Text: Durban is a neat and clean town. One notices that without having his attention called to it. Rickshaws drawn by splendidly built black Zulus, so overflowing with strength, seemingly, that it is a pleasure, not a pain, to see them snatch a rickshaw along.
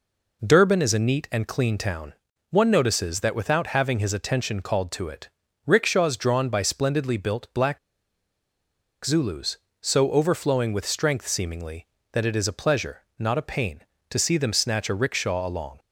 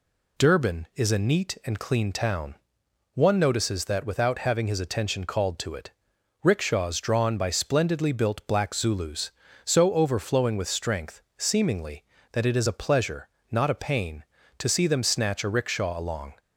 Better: second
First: pauses between "black" and "Zulus"; strong; at 7.7 s; 1.2 s long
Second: none

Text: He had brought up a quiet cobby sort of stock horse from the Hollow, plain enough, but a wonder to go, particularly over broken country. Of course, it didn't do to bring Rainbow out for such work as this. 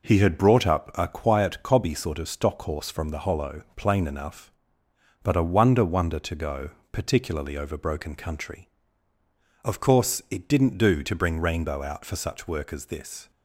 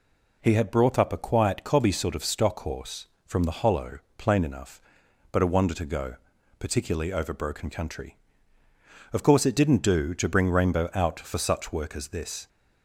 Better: second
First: says "wonder" twice; at 5.8 s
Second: none

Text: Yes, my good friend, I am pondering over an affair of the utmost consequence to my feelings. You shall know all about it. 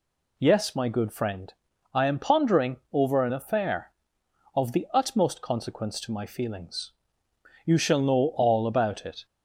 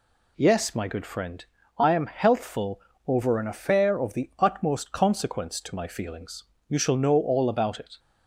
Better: first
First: none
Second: says "healthful" for "pondering"; at 2.0 s

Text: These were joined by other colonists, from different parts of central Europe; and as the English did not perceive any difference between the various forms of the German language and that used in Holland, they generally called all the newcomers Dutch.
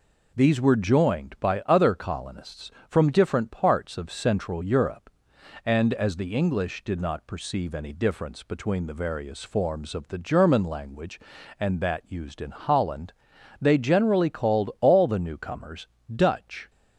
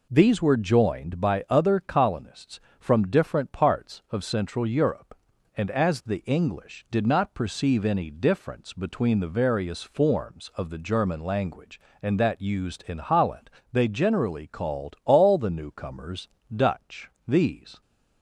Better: first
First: pauses between "newcomers" and "Dutch"; slight; at 15.8 s; 0.28 s long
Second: pauses between "newcomers" and "Dutch"; slight; at 16.2 s; 0.26 s long // goes on to say "These"; from 17.2 s on; 0.54 s long

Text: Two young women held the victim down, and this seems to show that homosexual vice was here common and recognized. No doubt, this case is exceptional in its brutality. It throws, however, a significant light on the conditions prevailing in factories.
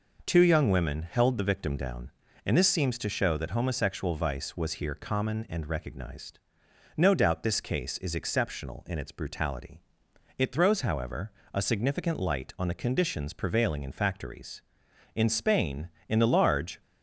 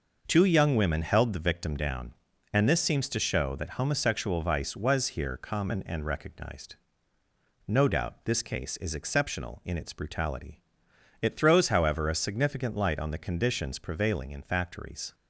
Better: second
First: goes on to say "In Spain in the large"; from 15.1 s on; 1.6 s long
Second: none

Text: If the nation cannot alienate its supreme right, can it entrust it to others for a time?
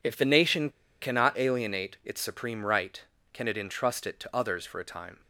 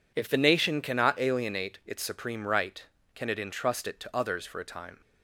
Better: second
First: pauses between "nation" and "cannot"; slight; at 0.7 s; 0.30 s long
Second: none

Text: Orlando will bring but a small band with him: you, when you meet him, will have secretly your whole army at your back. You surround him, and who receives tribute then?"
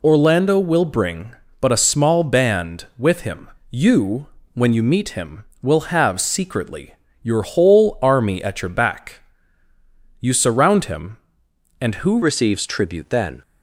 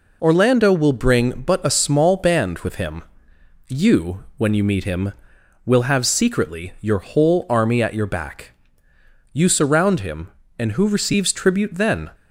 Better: second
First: pauses between "secretly" and "your"; slight; at 6.9 s; 0.28 s long // changes voice at "receives"; from 12.2 s on; 1.2 s long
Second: none

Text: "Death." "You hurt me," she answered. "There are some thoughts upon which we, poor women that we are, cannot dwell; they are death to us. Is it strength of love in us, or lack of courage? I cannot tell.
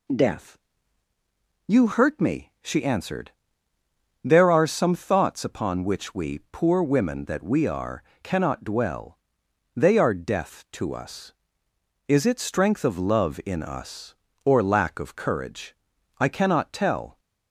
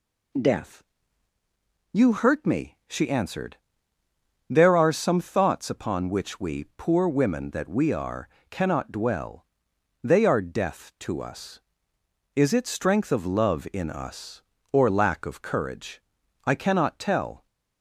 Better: neither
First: none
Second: none

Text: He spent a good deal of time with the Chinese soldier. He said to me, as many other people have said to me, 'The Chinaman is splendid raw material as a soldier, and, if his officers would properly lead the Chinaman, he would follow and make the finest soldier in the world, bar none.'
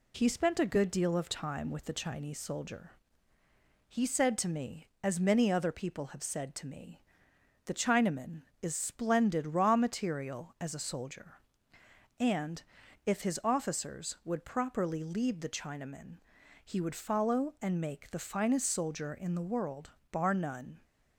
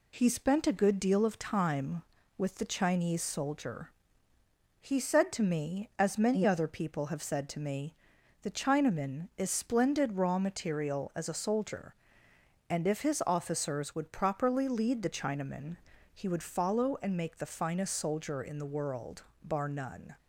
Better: neither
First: none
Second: none

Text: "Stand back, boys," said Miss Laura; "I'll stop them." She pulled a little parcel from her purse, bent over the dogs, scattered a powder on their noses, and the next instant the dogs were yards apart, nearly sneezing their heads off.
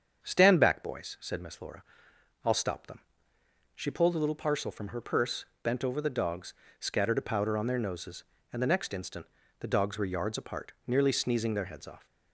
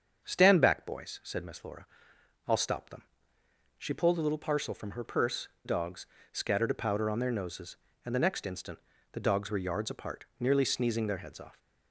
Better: first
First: starts louder than the rest; strong; until 1.2 s; 7.5 dB // pauses between "instant" and "the"; slight; at 9.2 s; 0.34 s long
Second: starts louder than the rest; strong; until 1.2 s; 7 dB // skips "bent over the"; at 5.5 s // pauses between "instant" and "the"; slight; at 8.7 s; 0.34 s long

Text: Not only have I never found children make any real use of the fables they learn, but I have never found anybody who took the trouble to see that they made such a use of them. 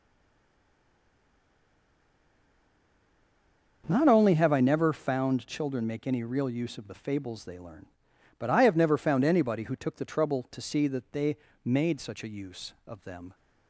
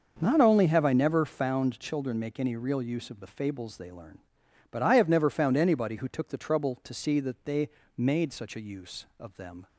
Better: second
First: stays silent before the first word; strong; until 3.8 s; 3.8 s long // starts louder than the rest; until 4.8 s; 6 dB // pauses between "they" and "made"; slight; at 11.3 s; 0.26 s long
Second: starts louder than the rest; until 1.2 s; 6 dB // pauses between "they" and "made"; slight; at 7.6 s; 0.26 s long

